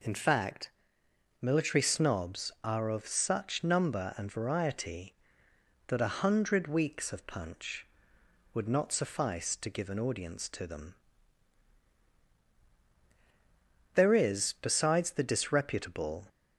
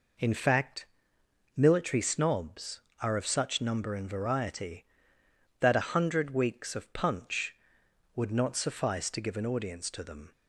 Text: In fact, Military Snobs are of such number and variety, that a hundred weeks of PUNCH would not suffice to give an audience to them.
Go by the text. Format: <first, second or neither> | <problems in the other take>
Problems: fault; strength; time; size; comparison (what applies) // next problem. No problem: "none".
second | goes on to say "There is besides the disreputable"; strong; from 13.9 s on; 2.3 s long